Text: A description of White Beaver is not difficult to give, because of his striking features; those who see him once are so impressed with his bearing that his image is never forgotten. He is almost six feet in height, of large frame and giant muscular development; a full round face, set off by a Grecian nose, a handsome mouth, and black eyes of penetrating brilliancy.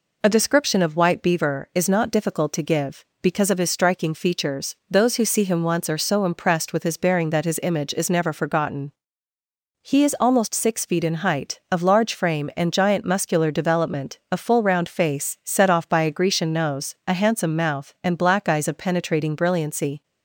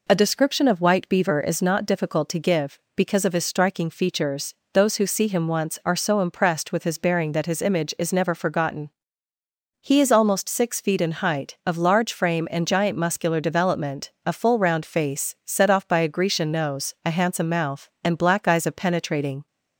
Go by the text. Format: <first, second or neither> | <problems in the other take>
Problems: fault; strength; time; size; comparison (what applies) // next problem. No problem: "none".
first | stops before "brilliancy"; at 19.4 s